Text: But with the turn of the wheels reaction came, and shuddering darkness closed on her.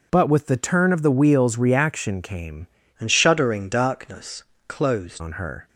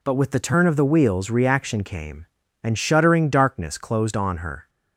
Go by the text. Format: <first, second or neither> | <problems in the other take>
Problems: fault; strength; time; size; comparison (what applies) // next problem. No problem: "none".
second | changes voice from "and" to "closed"; from 2.9 to 5.2 s; 2.3 s long // pauses between "darkness" and "closed"; slight; at 4.4 s; 0.26 s long